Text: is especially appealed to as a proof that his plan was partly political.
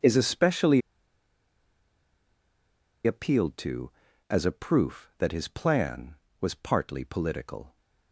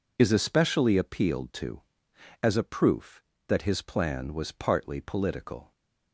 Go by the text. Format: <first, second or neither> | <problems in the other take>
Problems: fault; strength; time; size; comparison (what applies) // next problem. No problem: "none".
second | pauses between "especially" and "appealed"; strong; at 0.8 s; 2.2 s long